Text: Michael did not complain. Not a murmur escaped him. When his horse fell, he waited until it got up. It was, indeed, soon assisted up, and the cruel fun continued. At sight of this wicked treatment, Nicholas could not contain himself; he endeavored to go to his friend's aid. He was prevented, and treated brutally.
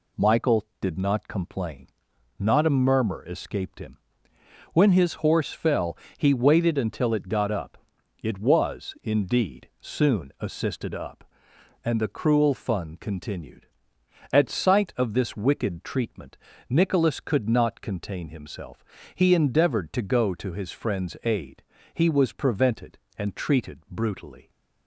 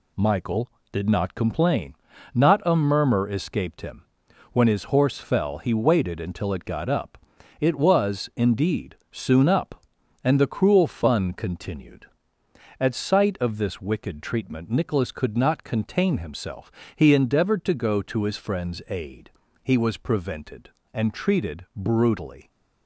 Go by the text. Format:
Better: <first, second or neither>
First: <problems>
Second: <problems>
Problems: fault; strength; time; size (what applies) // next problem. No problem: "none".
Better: first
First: none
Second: skips "assisted"; at 9.4 s